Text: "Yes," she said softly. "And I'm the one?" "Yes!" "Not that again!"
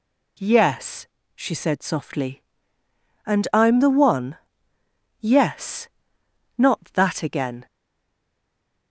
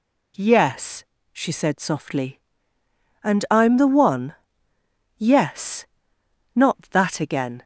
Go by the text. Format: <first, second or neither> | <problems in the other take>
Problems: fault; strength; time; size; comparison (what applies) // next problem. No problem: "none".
second | stays silent after the last word; noticeable; from 7.6 s on; 1.3 s long